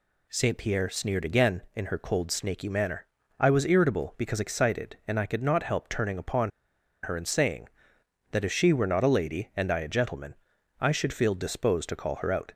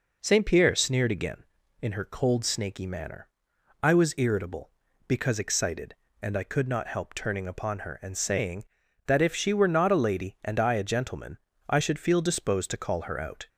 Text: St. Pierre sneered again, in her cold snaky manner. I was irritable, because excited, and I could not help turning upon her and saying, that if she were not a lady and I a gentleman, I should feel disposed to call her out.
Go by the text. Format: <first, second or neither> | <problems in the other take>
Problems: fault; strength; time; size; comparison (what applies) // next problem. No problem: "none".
second | pauses between "upon" and "her"; noticeable; at 6.5 s; 0.53 s long